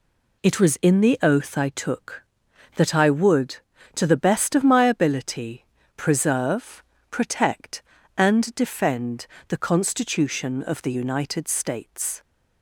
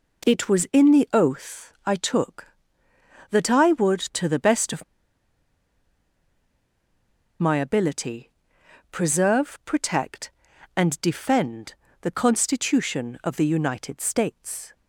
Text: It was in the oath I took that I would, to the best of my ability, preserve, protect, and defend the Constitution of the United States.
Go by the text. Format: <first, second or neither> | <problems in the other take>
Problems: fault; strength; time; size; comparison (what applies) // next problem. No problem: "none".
first | pauses between "of" and "my"; strong; at 4.8 s; 2.5 s long // pauses between "defend" and "the"; slight; at 11.7 s; 0.28 s long; slight in the first